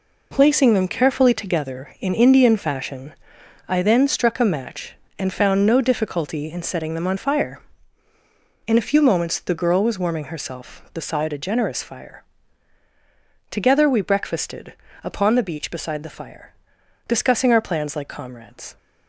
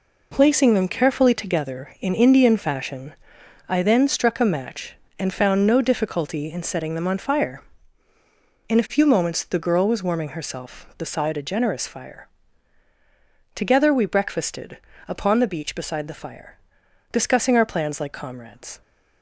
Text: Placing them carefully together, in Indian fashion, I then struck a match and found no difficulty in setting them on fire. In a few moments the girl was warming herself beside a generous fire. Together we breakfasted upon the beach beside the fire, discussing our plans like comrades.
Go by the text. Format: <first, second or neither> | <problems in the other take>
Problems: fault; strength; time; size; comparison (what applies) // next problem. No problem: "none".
neither | pauses between "breakfasted" and "upon"; slight; the same in both